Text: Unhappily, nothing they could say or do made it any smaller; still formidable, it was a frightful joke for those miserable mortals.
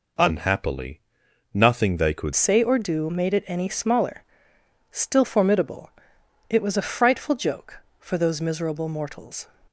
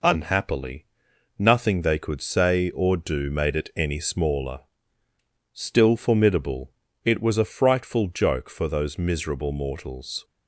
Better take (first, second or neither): second